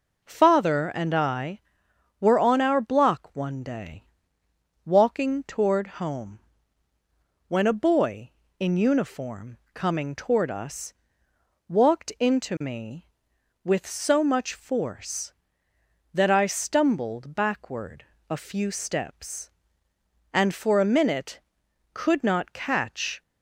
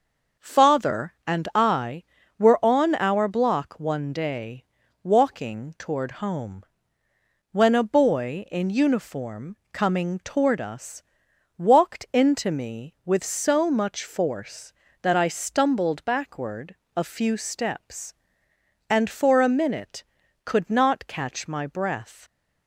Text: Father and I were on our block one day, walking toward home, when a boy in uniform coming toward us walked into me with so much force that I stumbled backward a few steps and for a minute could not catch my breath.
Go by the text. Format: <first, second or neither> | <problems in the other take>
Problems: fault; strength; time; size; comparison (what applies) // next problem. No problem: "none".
second | pauses between "uniform" and "coming"; slight; at 9.5 s; 0.16 s long; slight in the second // pauses between "us" and "walked"; noticeable; at 10.9 s; 0.76 s long; noticeable in the second // pauses between "backward" and "a"; slight; at 18.0 s; 0.26 s long; slight in the second // stops before "my breath"; at 23.2 s